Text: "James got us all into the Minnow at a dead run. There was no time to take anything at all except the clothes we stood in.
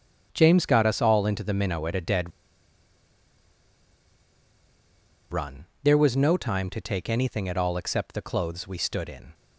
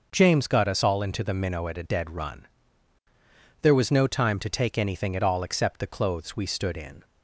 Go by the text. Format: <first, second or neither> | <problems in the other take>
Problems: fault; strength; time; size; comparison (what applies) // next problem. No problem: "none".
second | starts louder than the rest; strong; until 1.3 s; 8 dB; noticeable in the second // pauses between "dead" and "run"; strong; at 2.3 s; 3.0 s long